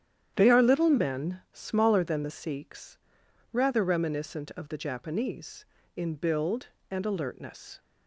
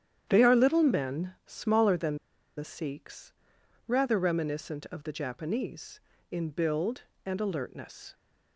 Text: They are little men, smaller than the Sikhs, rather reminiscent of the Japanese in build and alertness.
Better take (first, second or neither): first